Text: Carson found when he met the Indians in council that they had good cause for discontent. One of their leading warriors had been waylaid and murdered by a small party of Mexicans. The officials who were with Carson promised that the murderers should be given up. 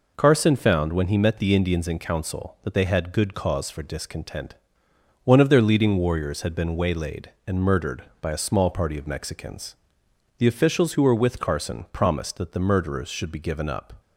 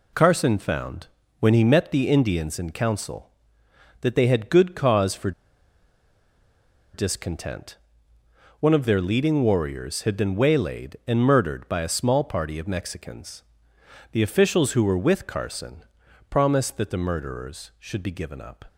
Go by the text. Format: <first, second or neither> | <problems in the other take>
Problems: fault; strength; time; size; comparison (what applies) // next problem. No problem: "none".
first | pauses between "found" and "when"; slight; at 1.0 s; 0.32 s long // pauses between "for" and "discontent"; strong; at 5.3 s; 1.6 s long // pauses between "Carson" and "promised"; noticeable; at 15.8 s; 0.46 s long